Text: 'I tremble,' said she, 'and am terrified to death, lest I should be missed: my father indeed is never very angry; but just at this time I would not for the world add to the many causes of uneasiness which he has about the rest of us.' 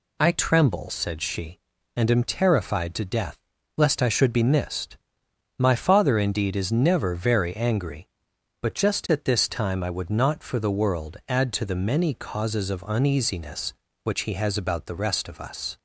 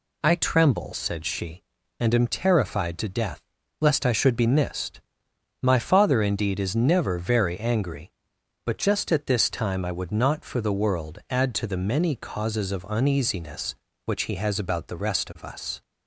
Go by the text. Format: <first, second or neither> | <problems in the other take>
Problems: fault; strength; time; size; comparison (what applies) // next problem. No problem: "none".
neither | none